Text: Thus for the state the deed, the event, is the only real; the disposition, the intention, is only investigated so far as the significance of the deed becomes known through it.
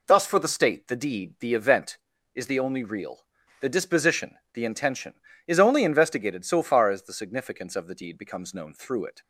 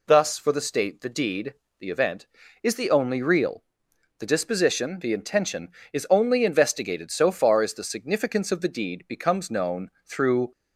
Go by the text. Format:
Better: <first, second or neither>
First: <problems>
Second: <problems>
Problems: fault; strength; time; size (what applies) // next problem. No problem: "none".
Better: first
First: none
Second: pauses between "known" and "through"; slight; at 9.8 s; 0.16 s long // stops before "it"; at 10.5 s